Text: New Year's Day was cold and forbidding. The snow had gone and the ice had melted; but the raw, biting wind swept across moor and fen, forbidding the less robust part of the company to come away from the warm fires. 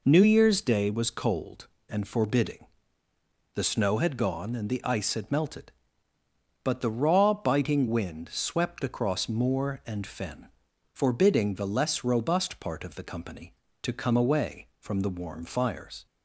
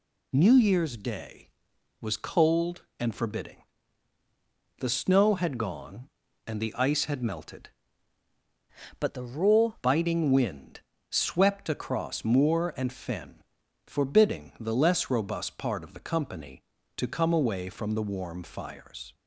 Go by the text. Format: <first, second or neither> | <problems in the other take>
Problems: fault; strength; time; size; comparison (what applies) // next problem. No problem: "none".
first | changes voice from "but" to "raw"; from 8.9 to 9.7 s; 0.8 s long // pauses between "wind" and "swept"; slight; at 10.7 s; 0.30 s long